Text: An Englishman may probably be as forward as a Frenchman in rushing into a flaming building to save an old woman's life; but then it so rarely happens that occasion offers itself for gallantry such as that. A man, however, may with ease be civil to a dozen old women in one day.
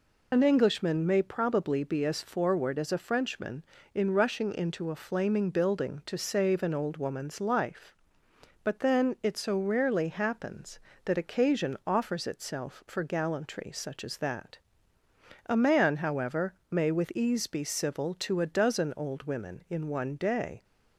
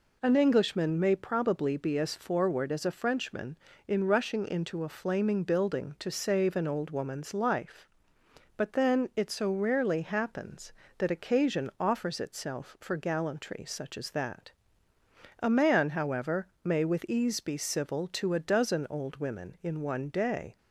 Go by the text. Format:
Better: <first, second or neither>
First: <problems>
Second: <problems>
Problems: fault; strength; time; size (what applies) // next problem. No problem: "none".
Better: second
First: loses the start of "An"; at 0.3 s; 45 ms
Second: none